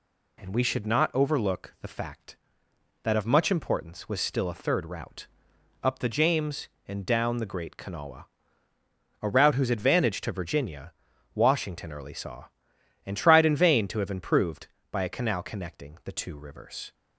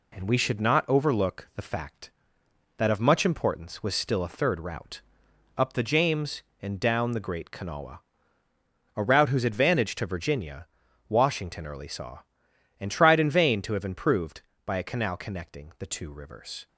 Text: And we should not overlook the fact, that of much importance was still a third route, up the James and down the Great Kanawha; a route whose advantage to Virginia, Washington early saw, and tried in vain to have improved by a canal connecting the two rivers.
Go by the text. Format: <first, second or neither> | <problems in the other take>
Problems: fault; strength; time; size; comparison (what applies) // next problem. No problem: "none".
first | gets quieter; slight; throughout; 3.5 dB